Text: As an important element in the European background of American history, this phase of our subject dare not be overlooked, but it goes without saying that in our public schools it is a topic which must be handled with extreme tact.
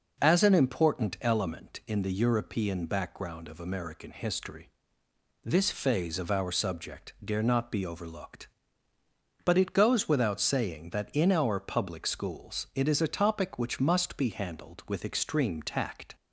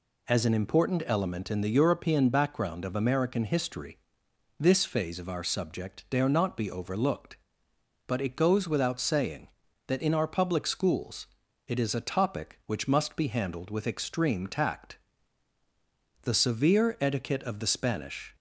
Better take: first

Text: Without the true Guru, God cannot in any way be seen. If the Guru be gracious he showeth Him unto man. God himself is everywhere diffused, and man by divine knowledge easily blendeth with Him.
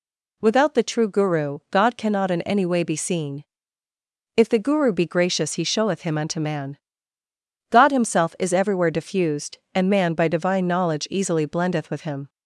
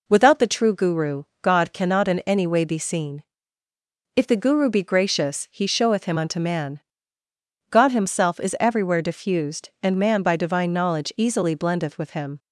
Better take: neither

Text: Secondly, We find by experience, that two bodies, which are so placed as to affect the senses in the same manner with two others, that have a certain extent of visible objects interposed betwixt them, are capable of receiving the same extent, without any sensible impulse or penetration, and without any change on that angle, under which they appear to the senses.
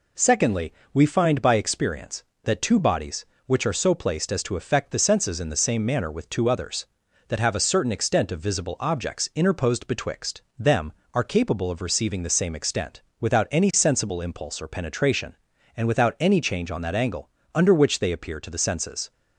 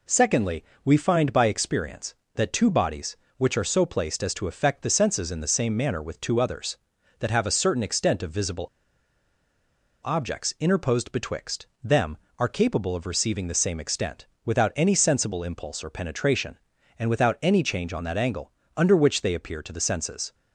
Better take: first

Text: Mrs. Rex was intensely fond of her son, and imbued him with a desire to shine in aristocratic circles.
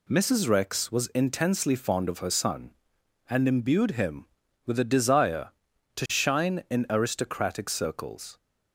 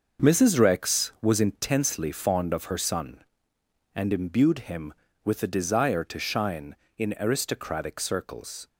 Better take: first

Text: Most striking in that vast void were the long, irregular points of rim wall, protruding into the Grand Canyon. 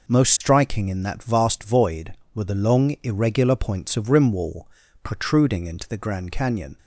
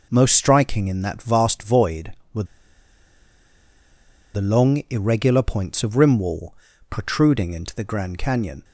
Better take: first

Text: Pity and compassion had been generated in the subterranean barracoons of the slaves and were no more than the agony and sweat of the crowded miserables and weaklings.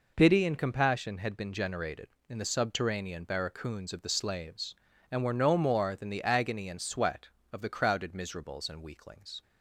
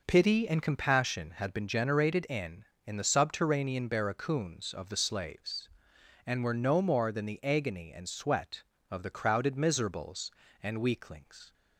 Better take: first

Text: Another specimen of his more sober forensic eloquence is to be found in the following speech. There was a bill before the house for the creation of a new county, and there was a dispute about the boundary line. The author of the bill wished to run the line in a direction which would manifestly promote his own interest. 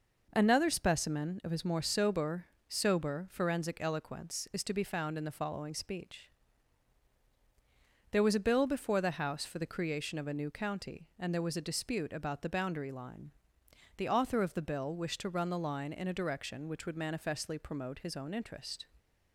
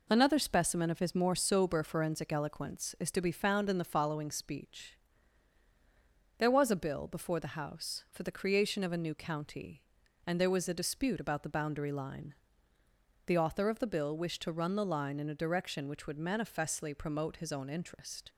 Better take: second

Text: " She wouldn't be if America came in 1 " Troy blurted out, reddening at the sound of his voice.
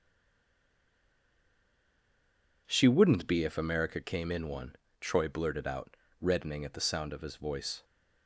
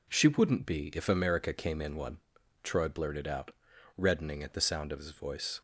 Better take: second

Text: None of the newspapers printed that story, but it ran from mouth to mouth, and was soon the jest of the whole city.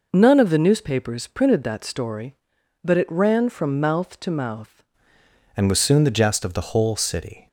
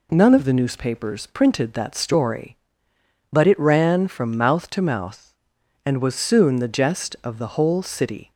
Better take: second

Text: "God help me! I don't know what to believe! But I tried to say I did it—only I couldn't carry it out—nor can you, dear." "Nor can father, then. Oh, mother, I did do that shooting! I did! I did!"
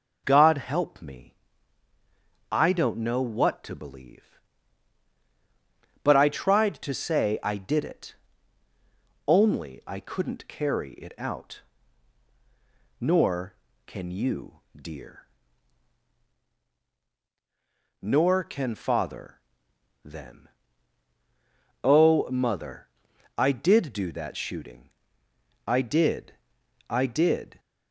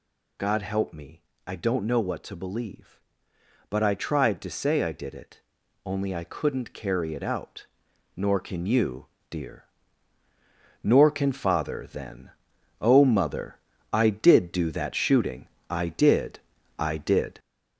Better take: first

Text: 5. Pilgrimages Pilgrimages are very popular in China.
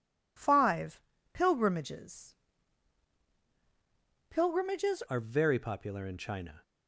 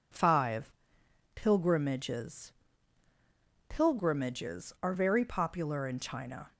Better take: second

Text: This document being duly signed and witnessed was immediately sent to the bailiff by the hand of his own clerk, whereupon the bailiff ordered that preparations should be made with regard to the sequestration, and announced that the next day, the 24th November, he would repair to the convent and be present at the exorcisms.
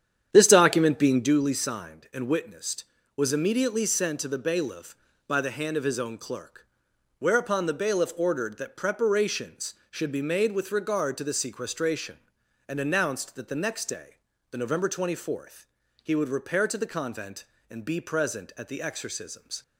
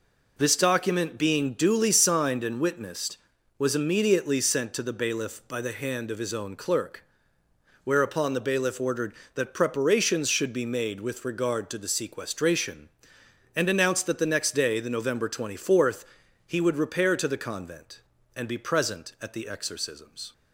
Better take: second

